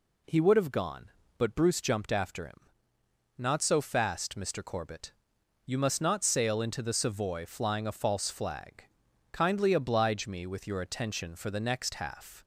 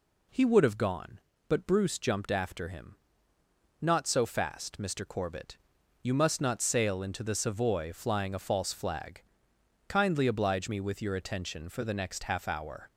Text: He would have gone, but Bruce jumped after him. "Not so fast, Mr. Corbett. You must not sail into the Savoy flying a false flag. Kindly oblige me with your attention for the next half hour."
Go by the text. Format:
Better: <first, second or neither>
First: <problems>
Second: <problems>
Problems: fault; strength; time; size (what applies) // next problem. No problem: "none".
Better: second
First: stops before "hour"; at 12.4 s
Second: none